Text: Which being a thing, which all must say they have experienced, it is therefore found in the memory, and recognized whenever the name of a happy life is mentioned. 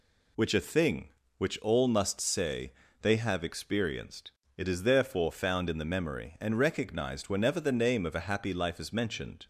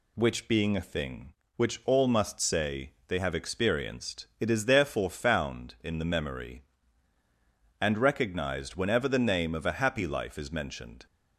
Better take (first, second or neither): second